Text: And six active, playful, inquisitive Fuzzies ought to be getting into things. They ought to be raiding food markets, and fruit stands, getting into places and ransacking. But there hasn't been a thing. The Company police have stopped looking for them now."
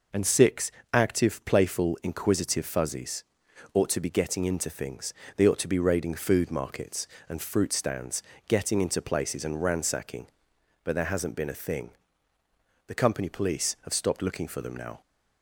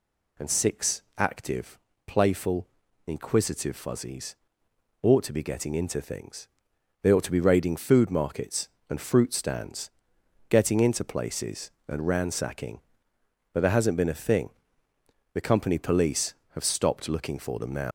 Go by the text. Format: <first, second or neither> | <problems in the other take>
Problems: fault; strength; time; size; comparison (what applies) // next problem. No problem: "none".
first | pauses between "six" and "active"; slight; at 1.0 s; 0.16 s long; slight in the first // pauses between "Fuzzies" and "ought"; noticeable; at 4.3 s; 0.66 s long; noticeable in the first // leaves "now" unfinished; at 17.8 s; 140 ms